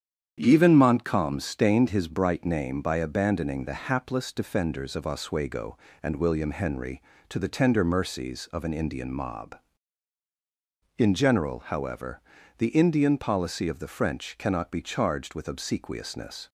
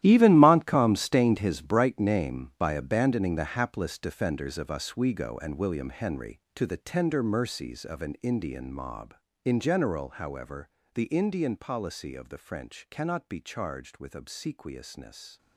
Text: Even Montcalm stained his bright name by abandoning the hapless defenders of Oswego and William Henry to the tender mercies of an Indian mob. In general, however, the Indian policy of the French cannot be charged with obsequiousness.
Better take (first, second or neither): first